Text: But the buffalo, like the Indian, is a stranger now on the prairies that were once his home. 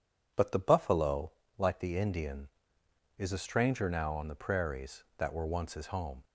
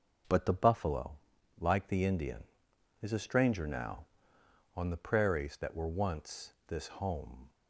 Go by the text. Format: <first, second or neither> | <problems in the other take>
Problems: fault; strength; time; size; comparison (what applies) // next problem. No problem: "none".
first | starts louder than the rest; noticeable; until 1.7 s; 6 dB // says "this" for "his"; at 6.6 s